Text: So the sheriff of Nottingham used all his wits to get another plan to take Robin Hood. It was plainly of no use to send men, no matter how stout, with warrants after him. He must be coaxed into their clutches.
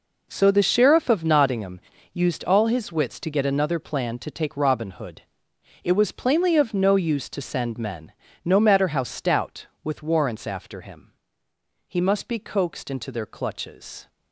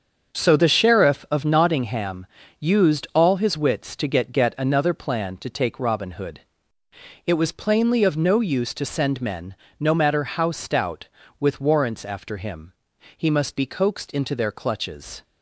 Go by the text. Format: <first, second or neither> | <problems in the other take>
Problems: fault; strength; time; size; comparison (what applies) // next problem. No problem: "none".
first | starts louder than the rest; until 1.4 s; 7 dB // pauses between "Nottingham" and "used"; slight; at 2.2 s; 0.32 s long; slight in the first // says "get" twice; at 4.3 s